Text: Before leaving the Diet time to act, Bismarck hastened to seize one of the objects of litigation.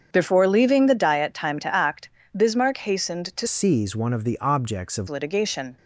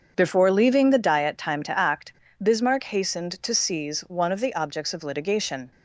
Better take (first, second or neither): second